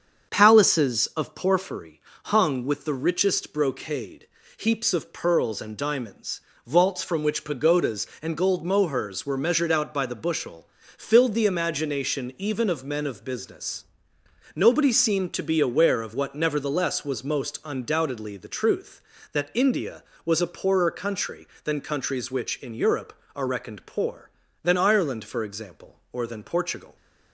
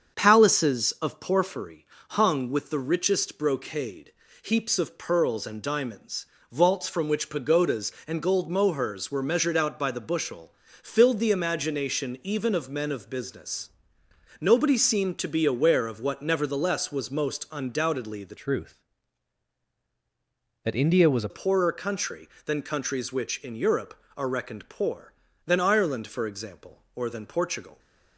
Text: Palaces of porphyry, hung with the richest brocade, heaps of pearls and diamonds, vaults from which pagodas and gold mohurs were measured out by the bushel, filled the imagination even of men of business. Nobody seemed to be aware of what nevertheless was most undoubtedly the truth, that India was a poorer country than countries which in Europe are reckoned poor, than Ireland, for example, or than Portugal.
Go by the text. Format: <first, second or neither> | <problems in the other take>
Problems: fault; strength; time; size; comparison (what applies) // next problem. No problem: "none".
first | starts louder than the rest; strong; until 1.2 s; 7 dB; strong in the first // changes voice from "truth" to "a"; from 18.3 to 21.2 s; 2.9 s long